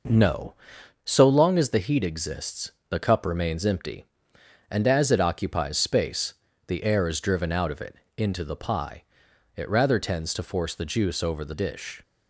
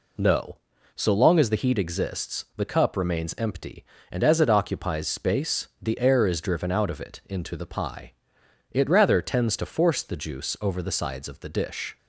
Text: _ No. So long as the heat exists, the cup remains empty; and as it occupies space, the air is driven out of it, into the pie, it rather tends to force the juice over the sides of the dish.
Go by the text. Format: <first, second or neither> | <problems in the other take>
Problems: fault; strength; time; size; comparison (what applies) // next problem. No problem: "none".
second | skips "sides of the"; at 11.5 s